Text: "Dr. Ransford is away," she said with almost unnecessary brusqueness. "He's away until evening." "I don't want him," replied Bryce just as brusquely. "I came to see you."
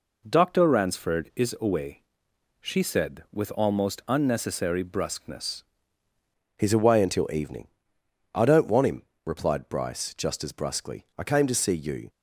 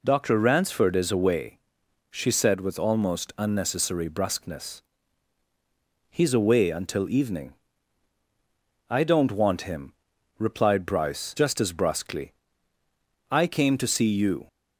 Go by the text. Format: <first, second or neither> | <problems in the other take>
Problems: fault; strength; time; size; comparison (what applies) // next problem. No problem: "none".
second | changes voice at "He's"; from 6.5 s on; 5.5 s long